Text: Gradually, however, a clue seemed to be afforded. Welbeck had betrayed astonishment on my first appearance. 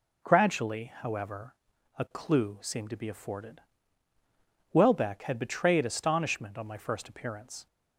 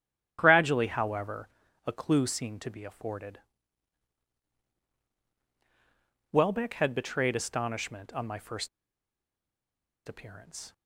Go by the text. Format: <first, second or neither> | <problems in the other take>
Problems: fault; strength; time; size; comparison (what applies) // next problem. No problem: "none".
first | starts louder than the rest; strong; until 1.4 s; 10.5 dB // pauses between "first" and "appearance"; strong; at 8.6 s; 1.4 s long